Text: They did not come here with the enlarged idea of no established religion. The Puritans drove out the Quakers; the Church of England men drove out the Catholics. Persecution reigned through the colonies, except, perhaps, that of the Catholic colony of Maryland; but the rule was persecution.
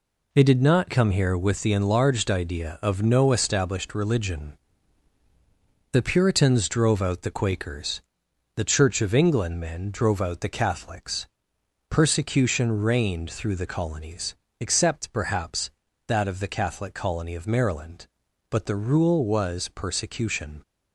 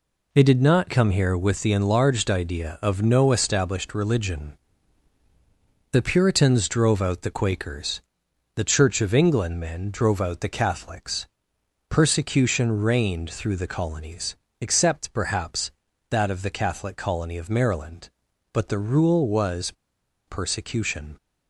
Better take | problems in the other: first | pauses between "was" and "persecution"; noticeable; at 19.7 s; 0.54 s long

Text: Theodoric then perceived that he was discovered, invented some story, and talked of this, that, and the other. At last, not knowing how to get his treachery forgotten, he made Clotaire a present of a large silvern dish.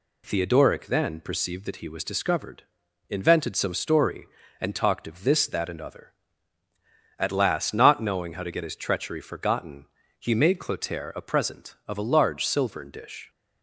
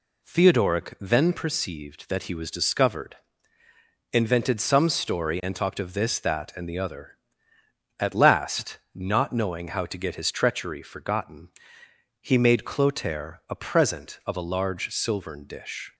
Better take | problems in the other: second | skips "the"; at 5.8 s

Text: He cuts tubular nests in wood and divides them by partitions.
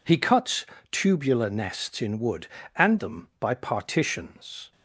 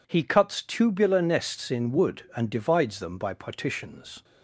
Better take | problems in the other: second | pauses between "cuts" and "tubular"; slight; at 0.6 s; 0.24 s long // skips "divides"; at 2.9 s

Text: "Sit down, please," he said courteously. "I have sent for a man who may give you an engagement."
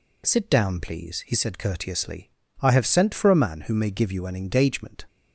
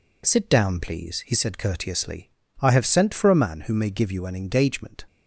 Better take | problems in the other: first | gets quieter; noticeable; throughout; 4.5 dB

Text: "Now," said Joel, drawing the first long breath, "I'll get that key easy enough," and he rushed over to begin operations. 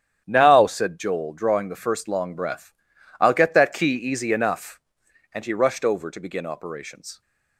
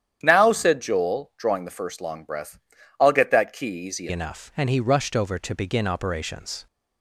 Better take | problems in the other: first | starts louder than the rest; strong; until 1.2 s; 9.5 dB; strong in the first // changes voice at "enough"; from 4.1 s on; 2.5 s long

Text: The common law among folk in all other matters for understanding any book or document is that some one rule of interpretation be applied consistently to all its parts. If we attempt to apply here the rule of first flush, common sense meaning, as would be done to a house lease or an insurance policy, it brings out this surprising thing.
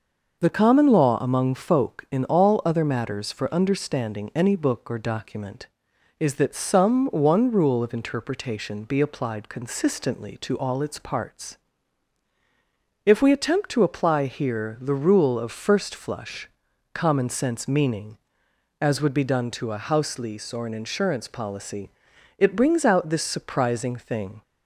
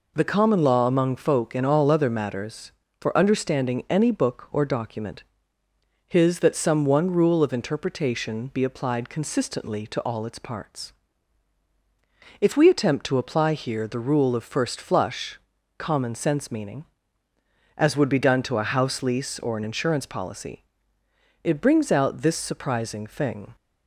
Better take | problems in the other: first | says "his" for "is"; at 6.0 s

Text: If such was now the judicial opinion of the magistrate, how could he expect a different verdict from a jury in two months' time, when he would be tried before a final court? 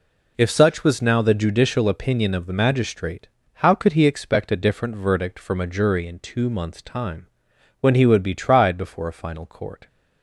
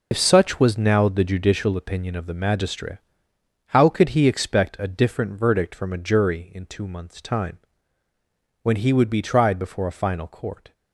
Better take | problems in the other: first | loses the start of "If"; at 0.1 s; 70 ms

